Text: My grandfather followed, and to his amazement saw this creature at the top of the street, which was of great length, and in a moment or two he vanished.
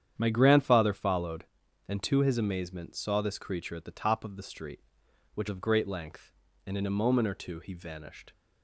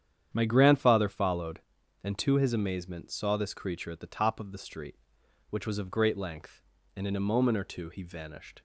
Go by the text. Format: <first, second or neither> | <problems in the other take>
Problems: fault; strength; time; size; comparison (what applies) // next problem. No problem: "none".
second | starts louder than the rest; strong; until 1.1 s; 9 dB; strong in the second // skips "was"; at 5.4 s